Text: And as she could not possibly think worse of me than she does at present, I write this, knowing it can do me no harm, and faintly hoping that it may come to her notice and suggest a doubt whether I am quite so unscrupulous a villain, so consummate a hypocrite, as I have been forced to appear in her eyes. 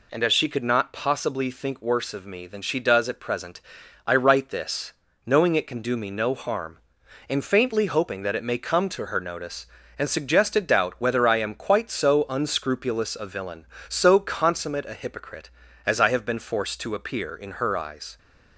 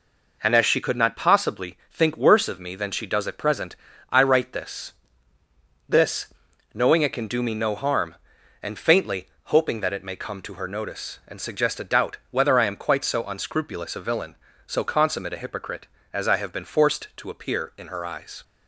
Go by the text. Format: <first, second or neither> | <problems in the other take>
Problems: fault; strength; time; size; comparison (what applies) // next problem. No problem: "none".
first | says "this" twice; at 5.8 s // pauses between "faintly" and "hoping"; slight; at 9.2 s; 0.18 s long